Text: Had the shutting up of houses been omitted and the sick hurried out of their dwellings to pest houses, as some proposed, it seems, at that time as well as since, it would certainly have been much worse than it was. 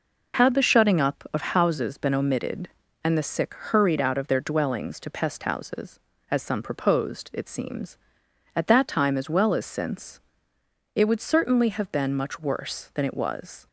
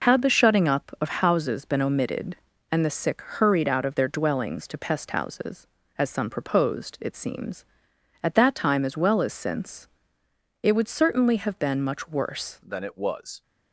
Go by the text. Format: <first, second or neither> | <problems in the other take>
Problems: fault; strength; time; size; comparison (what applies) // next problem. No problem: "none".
first | changes voice at "than"; from 12.6 s on; 0.8 s long